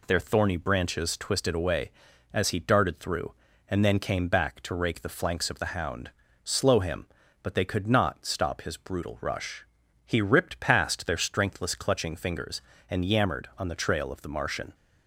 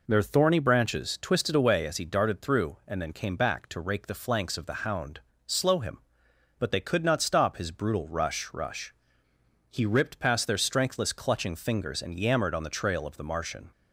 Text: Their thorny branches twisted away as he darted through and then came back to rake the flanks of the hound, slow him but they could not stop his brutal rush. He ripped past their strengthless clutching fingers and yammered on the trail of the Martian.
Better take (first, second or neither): first